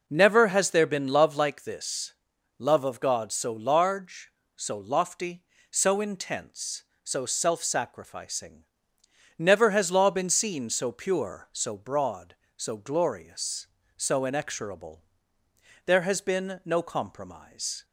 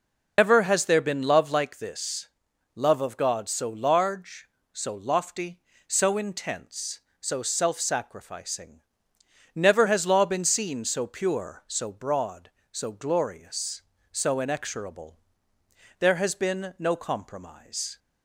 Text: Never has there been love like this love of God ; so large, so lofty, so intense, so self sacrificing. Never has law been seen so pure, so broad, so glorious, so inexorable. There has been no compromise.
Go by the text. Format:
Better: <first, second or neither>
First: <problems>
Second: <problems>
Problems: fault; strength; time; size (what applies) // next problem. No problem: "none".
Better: first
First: pauses between "this" and "love"; noticeable; at 2.1 s; 0.46 s long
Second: loses the start of "Never"; at 0.3 s; 150 ms // pauses between "this" and "love"; noticeable; at 2.2 s; 0.48 s long